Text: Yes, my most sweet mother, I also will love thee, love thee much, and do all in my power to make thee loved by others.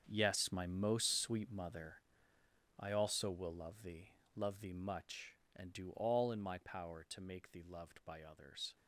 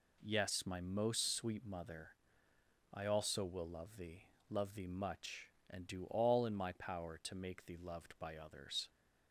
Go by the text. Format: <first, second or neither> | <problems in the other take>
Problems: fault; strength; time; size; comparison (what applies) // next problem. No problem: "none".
second | gets quieter; strong; throughout; 13 dB